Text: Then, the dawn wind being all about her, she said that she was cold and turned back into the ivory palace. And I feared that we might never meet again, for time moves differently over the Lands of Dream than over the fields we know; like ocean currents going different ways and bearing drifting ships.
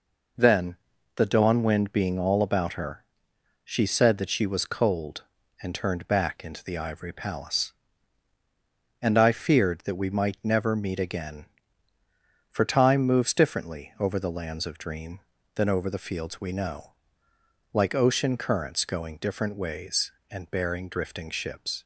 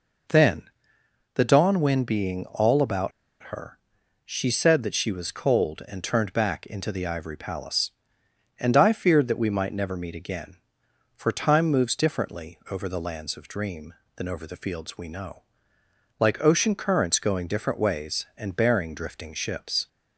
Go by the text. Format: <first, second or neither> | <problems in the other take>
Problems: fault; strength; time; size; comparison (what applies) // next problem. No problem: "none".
first | pauses between "about" and "her"; at 3.1 s; 0.36 s long